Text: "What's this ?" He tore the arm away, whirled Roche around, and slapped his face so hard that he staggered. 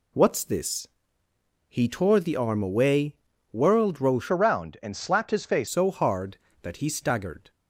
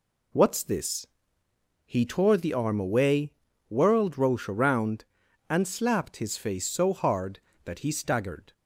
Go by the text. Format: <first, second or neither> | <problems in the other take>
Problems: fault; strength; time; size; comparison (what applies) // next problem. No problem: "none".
second | changes voice from "around" to "face"; from 4.3 to 5.6 s; 1.3 s long